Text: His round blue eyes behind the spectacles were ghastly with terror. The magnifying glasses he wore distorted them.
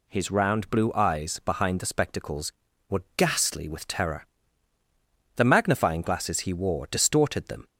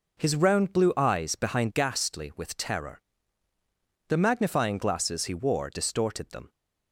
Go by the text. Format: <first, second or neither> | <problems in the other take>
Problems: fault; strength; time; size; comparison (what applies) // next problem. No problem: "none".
first | skips "the spectacles were"; at 1.7 s